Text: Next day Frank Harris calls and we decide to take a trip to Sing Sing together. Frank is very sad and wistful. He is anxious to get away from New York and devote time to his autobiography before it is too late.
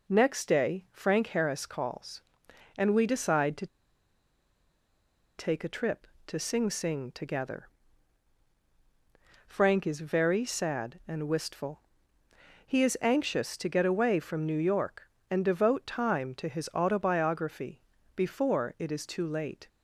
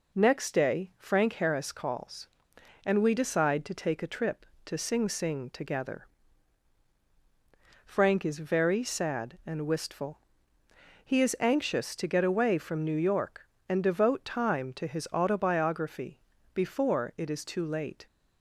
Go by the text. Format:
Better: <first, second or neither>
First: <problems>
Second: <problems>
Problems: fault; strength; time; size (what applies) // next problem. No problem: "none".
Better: second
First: pauses between "to" and "take"; strong; at 3.6 s; 1.7 s long // pauses between "autobiography" and "before"; slight; at 17.8 s; 0.34 s long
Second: pauses between "autobiography" and "before"; slight; at 16.1 s; 0.34 s long